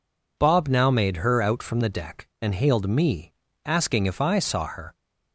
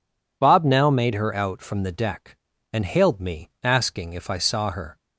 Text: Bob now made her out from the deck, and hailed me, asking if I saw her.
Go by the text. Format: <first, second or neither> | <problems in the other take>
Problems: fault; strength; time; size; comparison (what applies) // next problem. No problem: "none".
neither | none